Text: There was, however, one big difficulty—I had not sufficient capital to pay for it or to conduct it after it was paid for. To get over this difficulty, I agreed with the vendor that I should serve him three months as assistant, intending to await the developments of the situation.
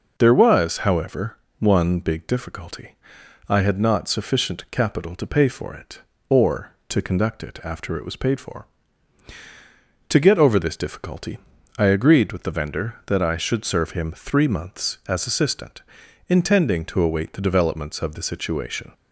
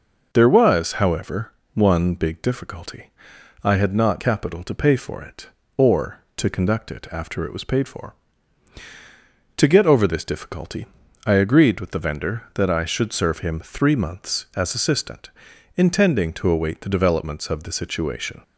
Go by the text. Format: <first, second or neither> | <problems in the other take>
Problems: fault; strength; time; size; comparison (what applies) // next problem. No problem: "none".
first | skips "sufficient"; at 4.2 s